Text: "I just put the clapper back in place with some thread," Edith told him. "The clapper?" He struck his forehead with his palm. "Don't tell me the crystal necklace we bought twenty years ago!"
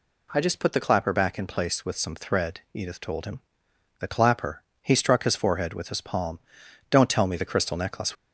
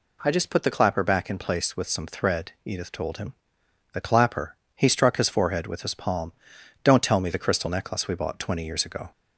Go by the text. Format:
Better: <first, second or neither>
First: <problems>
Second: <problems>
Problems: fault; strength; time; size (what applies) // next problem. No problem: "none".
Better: second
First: stops before "we bought twenty years ago"; at 8.1 s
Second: none